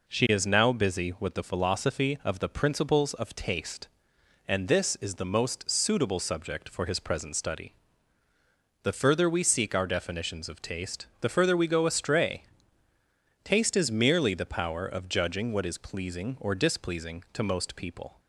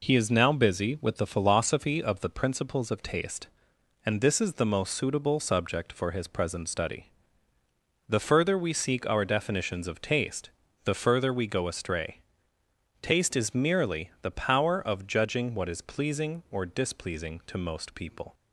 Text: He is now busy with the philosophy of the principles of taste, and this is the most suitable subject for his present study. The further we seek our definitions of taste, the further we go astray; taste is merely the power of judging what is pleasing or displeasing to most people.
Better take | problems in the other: second | says "She" for "He"; at 0.0 s

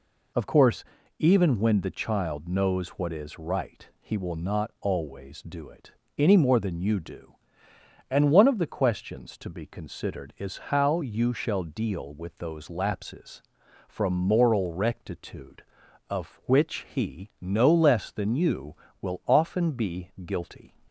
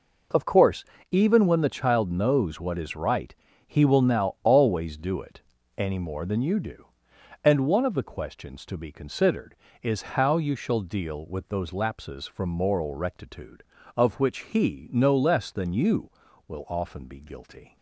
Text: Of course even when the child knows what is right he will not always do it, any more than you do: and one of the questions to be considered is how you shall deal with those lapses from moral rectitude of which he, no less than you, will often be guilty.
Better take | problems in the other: first | pauses between "course" and "even"; slight; at 0.8 s; 0.26 s long; slight in the first // pauses between "right" and "he"; slight; at 3.3 s; 0.34 s long // says "now" for "not"; at 4.0 s

